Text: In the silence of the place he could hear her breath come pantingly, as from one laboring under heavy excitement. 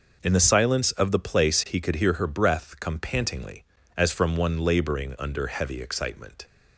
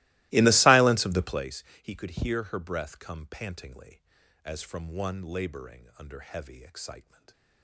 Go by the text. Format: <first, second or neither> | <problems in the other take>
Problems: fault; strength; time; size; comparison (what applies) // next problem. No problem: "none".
first | starts louder than the rest; strong; until 1.5 s; 20 dB // pauses between "place" and "he"; slight; at 1.6 s; 0.18 s long